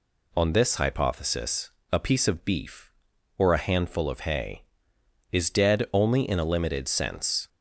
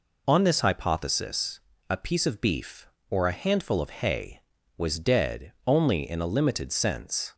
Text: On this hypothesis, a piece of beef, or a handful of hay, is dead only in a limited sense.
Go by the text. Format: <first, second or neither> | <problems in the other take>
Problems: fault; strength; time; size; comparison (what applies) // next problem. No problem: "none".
first | says "was" for "is"; at 4.7 s